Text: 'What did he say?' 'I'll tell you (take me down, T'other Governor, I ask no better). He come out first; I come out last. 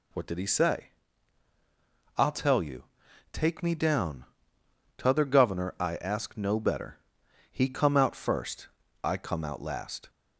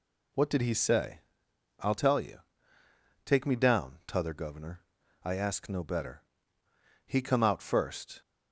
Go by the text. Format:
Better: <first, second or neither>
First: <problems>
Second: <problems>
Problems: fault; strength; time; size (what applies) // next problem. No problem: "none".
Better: first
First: none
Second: stops before "I come out last"; at 8.2 s